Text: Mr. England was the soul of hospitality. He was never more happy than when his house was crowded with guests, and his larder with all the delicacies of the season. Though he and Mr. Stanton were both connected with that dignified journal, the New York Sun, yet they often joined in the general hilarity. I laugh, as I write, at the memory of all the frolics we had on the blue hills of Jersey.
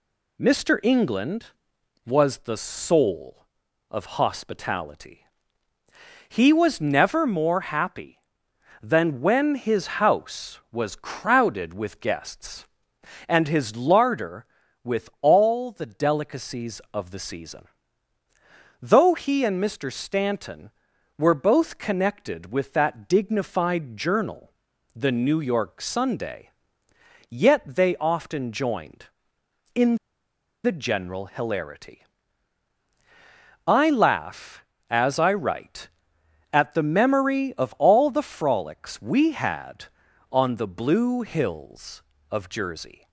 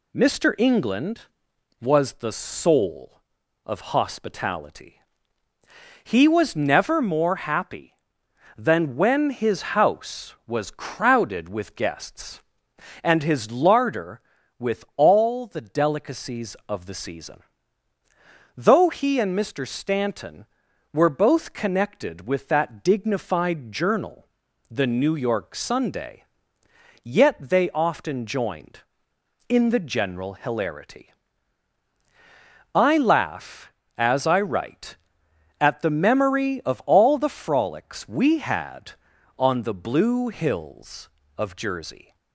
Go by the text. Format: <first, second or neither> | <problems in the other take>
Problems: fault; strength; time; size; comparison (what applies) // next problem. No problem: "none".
second | pauses between "his" and "house"; slight; at 9.8 s; 0.16 s long; slight in the second // pauses between "in" and "the"; noticeable; at 29.9 s; 0.69 s long